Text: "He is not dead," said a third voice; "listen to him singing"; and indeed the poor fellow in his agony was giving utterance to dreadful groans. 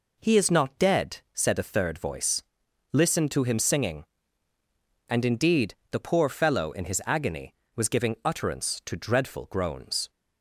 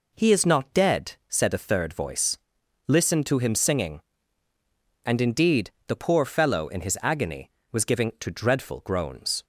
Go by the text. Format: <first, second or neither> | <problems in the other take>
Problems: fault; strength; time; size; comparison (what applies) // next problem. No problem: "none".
first | pauses between "indeed" and "the"; slight; at 5.7 s; 0.16 s long; slight in the first // skips "utterance"; at 8.1 s